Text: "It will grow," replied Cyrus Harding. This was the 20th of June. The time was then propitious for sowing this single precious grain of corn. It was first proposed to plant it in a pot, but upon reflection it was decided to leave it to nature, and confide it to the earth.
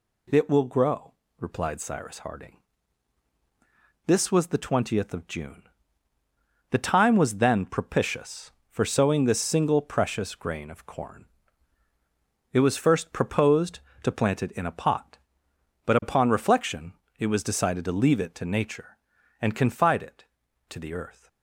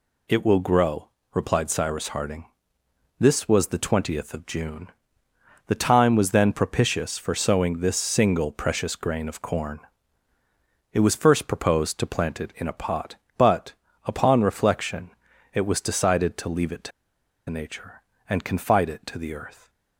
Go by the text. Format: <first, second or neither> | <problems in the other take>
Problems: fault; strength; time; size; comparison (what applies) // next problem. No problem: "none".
first | pauses between "but" and "upon"; slight; at 13.7 s; 0.32 s long // pauses between "reflection" and "it"; at 15.0 s; 0.44 s long; slight in the first // pauses between "to" and "nature"; noticeable; at 16.9 s; 0.58 s long